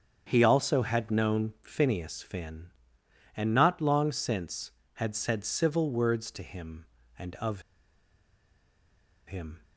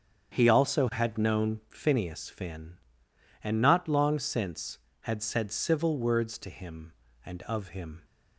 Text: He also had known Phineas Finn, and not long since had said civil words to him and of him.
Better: second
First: starts louder than the rest; strong; until 1.2 s; 8 dB // pauses between "of" and "him"; strong; at 7.6 s; 1.6 s long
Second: starts louder than the rest; strong; until 1.3 s; 8 dB

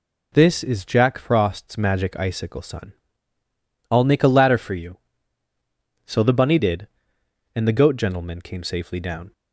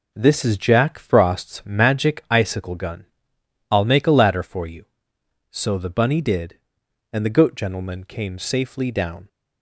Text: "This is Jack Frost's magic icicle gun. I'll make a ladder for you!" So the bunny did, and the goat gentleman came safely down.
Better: second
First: says "sun" for "gun"; at 2.6 s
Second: none

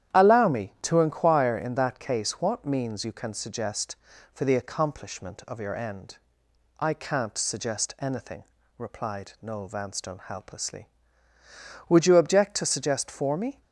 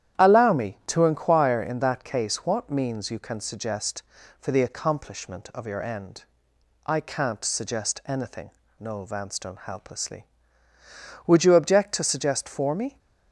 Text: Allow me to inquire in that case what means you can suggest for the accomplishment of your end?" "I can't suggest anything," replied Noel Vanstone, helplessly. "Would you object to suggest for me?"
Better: first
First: starts louder than the rest; strong; until 1.2 s; 10.5 dB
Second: starts louder than the rest; strong; until 1.2 s; 10.5 dB // skips "replied"; at 8.6 s

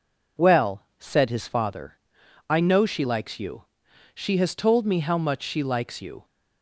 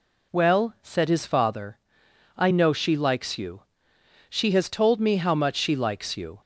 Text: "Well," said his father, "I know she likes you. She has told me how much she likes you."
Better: neither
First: none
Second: none

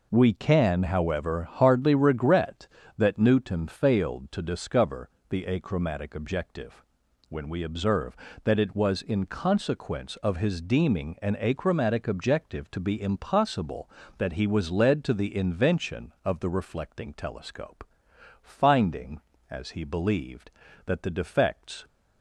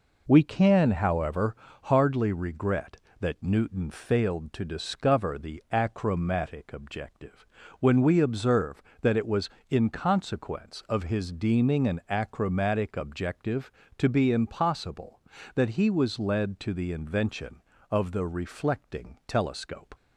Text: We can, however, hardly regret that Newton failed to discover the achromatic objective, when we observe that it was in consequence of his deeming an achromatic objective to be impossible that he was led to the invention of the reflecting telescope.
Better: second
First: pauses between "discover" and "the"; slight; at 5.0 s; 0.20 s long // goes on to say "Finding as he believed that the defects"; strong; from 18.4 s on; 3.4 s long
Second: none

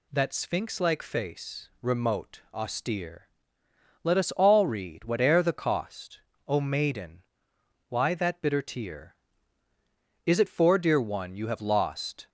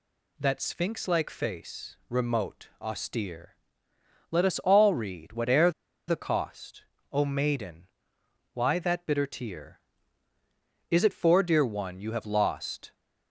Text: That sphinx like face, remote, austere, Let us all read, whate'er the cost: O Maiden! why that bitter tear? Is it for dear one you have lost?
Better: first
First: none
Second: pauses between "whate'er" and "the"; at 5.6 s; 0.38 s long

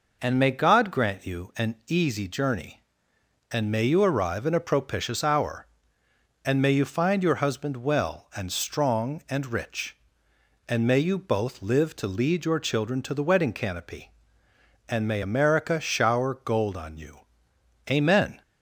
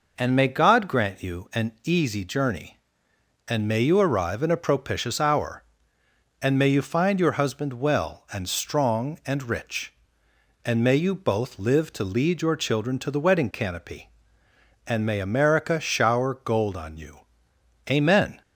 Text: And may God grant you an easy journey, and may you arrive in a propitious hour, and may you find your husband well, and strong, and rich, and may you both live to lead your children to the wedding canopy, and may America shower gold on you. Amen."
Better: neither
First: none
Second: none

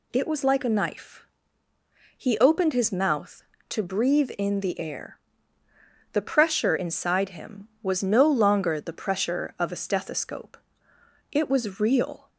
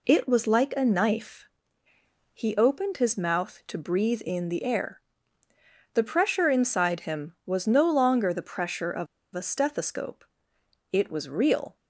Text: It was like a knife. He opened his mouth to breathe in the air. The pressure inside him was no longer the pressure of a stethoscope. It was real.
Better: first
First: none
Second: pauses between "of" and "a"; slight; at 9.0 s; 0.29 s long

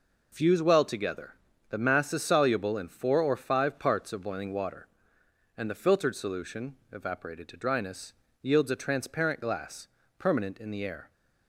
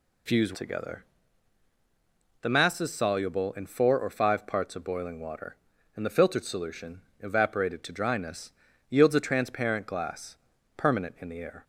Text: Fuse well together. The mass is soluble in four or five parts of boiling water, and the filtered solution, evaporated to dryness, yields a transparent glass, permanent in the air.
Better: first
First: none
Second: skips "well"; at 0.5 s

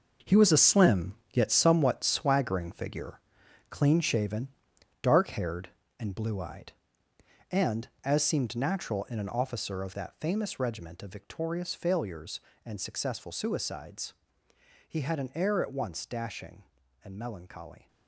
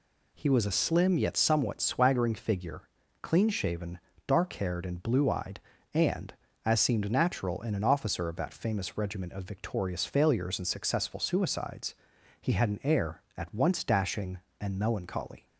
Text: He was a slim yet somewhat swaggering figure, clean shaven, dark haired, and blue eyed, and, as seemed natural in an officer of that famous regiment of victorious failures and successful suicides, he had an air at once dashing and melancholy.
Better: second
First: gets quieter; strong; throughout; 10.5 dB // pauses between "slim" and "yet"; slight; at 1.1 s; 0.18 s long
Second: none

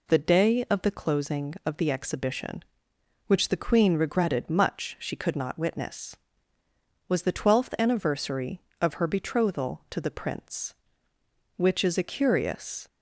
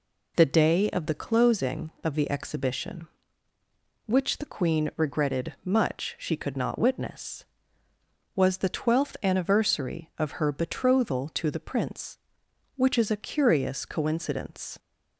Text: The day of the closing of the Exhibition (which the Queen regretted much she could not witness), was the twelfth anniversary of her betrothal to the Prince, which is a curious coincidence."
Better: second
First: stops before "coincidence"; at 12.8 s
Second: none

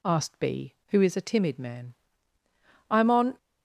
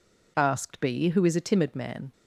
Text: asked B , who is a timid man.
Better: second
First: goes on to say "I am on"; slight; from 2.8 s on; 0.48 s long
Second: none

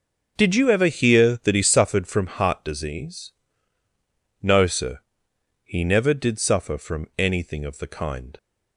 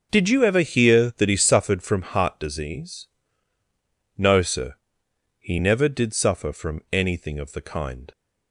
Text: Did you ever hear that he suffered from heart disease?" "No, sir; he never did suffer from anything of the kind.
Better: neither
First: starts louder than the rest; until 1.3 s; 6.5 dB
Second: starts louder than the rest; noticeable; until 1.1 s; 6 dB

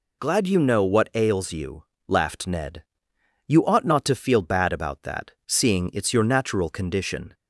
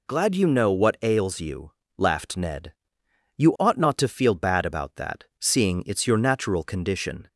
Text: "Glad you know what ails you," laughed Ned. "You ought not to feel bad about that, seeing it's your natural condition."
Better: neither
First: none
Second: none

